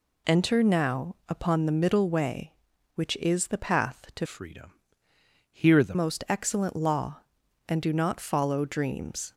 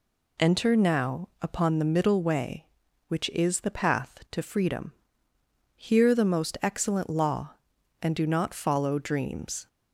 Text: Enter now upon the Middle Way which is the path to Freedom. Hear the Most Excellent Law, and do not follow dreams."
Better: second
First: changes voice from "Freedom" to "the"; from 4.2 to 5.9 s; 1.7 s long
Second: none

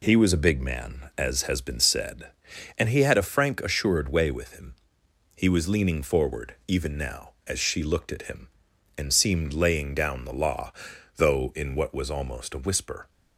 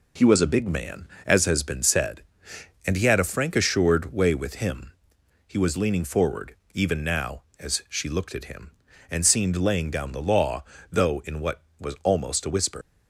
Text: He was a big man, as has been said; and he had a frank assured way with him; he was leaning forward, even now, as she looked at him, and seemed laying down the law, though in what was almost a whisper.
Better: first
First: none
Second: leaves "whisper" unfinished; at 12.8 s; 115 ms

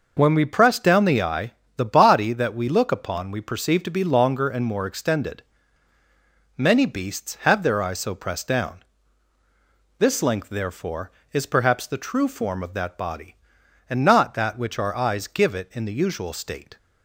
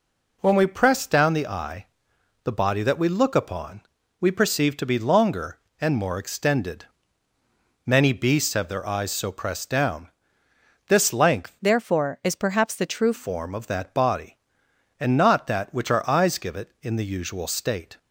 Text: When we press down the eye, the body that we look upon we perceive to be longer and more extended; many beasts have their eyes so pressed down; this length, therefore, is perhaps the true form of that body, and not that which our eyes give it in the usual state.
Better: first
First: none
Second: pauses between "upon" and "we"; at 3.8 s; 0.40 s long // changes voice from "therefore" to "true"; from 11.6 to 13.1 s; 1.5 s long

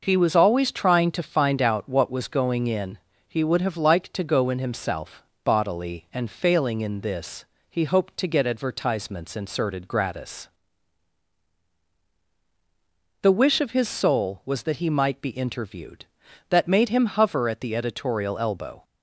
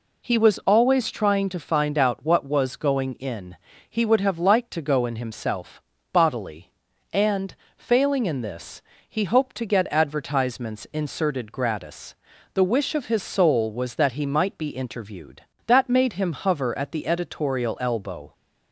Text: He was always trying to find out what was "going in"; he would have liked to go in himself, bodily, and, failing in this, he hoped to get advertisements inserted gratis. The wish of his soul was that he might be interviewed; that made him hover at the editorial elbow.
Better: neither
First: none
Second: none

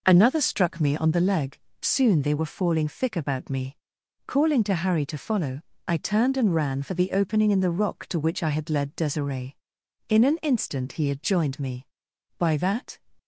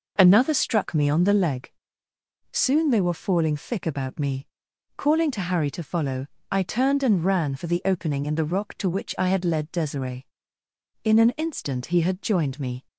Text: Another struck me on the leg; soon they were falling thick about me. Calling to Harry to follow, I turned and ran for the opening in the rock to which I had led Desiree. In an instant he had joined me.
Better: second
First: goes on to say "By that"; from 12.3 s on; 0.58 s long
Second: none

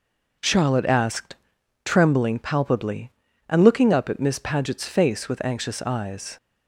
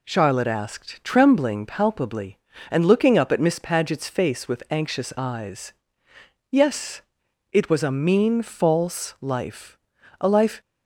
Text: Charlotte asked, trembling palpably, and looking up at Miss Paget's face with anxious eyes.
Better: first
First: none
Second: goes on to say "Yes it was a mean false life a life"; strong; from 6.4 s on; 4.1 s long

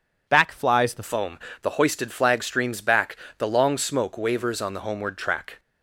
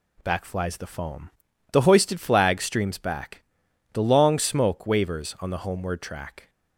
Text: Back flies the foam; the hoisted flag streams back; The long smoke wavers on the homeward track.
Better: second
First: changes voice at "foam"; from 1.0 s on; 4.5 s long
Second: none

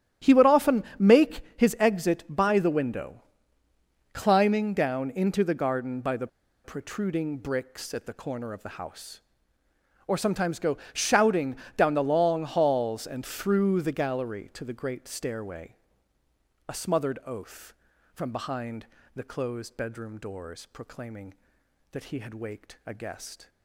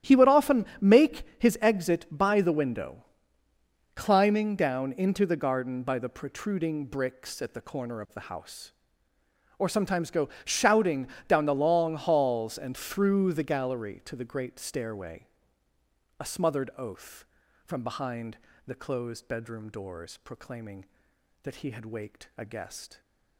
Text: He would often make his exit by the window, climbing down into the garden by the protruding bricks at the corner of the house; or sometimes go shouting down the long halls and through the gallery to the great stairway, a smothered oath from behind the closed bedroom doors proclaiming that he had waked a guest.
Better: second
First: starts louder than the rest; strong; until 1.3 s; 11.5 dB // pauses between "often" and "make"; slight; at 0.8 s; 0.16 s long // pauses between "make" and "his"; slight; at 1.4 s; 0.16 s long // pauses between "the" and "protruding"; slight; at 6.2 s; 0.35 s long // pauses between "go" and "shouting"; slight; at 10.7 s; 0.16 s long // pauses between "shouting" and "down"; slight; at 11.5 s; 0.20 s long // pauses between "behind" and "the"; slight; at 18.8 s; 0.28 s long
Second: starts louder than the rest; strong; until 1.2 s; 11.5 dB // pauses between "often" and "make"; slight; at 0.6 s; 0.16 s long // pauses between "make" and "his"; slight; at 1.2 s; 0.16 s long // pauses between "go" and "shouting"; slight; at 10.3 s; 0.16 s long // pauses between "shouting" and "down"; slight; at 11.0 s; 0.20 s long // pauses between "behind" and "the"; slight; at 18.3 s; 0.28 s long

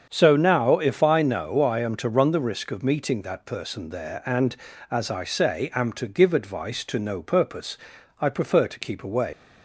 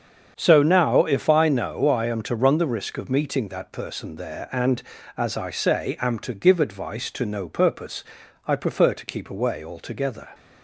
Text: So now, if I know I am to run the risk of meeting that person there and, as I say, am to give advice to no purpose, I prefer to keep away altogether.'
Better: second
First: starts louder than the rest; strong; until 1.1 s; 7 dB // stops before "altogether"; at 9.3 s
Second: starts louder than the rest; strong; until 1.3 s; 7 dB

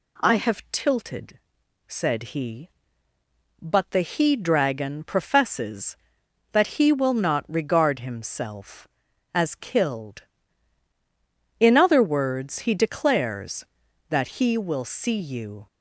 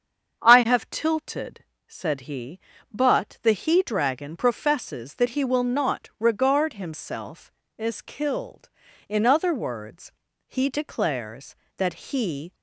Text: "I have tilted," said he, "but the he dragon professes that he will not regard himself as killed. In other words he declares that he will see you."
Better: first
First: none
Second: starts louder than the rest; strong; until 1.4 s; 7.5 dB // pauses between "words" and "he"; slight; at 10.1 s; 0.36 s long // stops before "will see you"; at 12.5 s

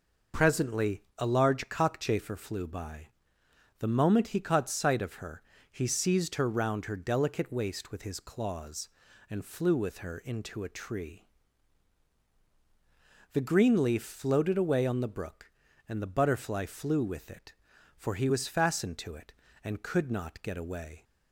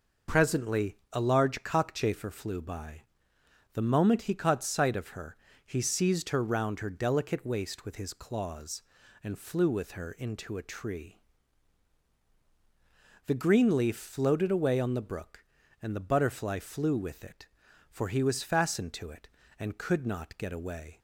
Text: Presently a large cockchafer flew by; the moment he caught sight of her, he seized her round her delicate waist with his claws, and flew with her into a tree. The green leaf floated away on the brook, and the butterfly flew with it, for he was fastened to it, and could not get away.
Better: neither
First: pauses between "Presently" and "a"; slight; at 1.0 s; 0.16 s long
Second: pauses between "Presently" and "a"; slight; at 0.9 s; 0.16 s long

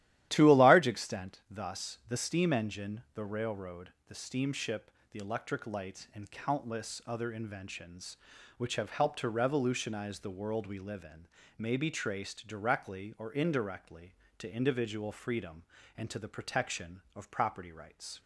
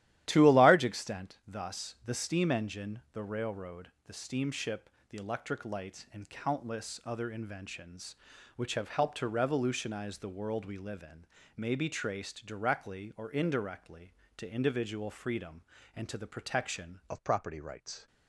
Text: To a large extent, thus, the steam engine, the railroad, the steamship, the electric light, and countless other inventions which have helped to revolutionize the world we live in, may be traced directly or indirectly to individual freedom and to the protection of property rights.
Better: first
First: starts louder than the rest; strong; until 1.3 s; 13 dB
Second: starts louder than the rest; strong; until 1.2 s; 13.5 dB // changes voice at "of"; from 17.0 s on; 1.0 s long

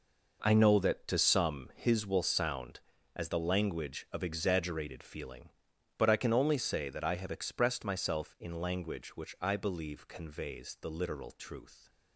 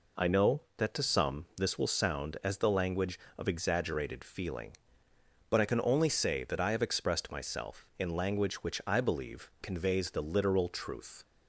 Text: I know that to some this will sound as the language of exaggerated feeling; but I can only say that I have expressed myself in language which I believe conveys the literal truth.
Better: second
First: says "his" for "this"; at 1.7 s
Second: none

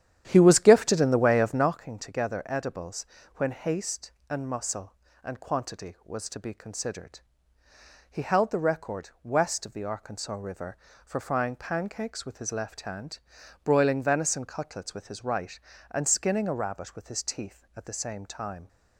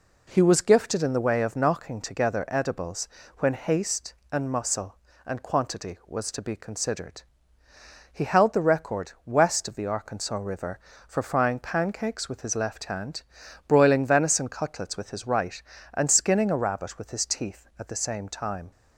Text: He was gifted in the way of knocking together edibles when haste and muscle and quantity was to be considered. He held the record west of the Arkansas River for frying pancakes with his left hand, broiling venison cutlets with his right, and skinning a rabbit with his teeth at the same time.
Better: second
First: starts louder than the rest; strong; until 1.7 s; 10.5 dB // pauses between "edibles" and "when"; slight; at 3.0 s; 0.30 s long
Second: pauses between "edibles" and "when"; slight; at 3.0 s; 0.30 s long

